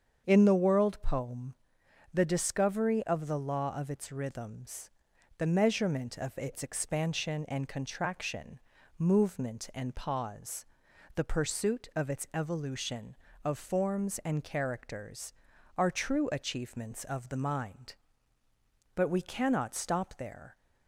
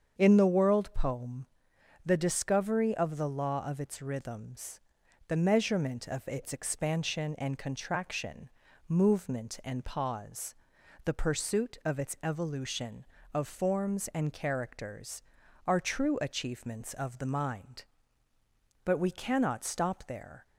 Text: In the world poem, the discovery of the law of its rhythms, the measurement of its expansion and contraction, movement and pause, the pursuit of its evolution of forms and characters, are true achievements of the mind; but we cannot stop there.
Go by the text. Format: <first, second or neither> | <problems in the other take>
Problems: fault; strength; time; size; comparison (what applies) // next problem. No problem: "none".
neither | starts louder than the rest; strong; the same in both